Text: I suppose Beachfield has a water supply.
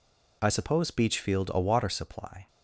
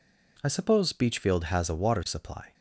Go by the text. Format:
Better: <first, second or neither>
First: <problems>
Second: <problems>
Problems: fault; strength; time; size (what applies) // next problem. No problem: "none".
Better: second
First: skips "has"; at 1.4 s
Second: none